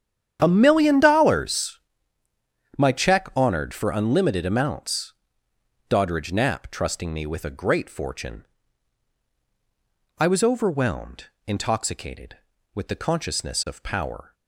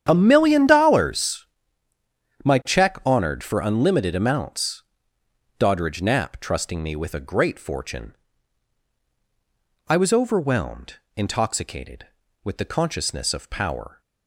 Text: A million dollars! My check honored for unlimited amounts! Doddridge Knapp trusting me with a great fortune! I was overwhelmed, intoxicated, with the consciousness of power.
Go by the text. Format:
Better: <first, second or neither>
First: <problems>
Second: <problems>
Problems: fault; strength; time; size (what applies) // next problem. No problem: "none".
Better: neither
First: starts louder than the rest; strong; until 1.4 s; 9 dB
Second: starts louder than the rest; strong; until 1.1 s; 9 dB